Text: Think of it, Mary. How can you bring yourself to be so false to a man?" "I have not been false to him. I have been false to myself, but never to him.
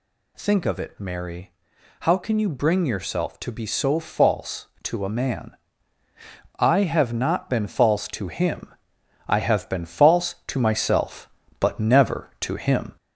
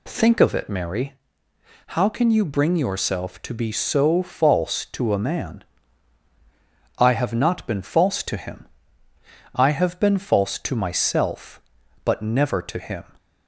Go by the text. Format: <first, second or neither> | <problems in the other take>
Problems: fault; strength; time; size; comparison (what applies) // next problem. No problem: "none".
second | gets louder; slight; throughout; 3 dB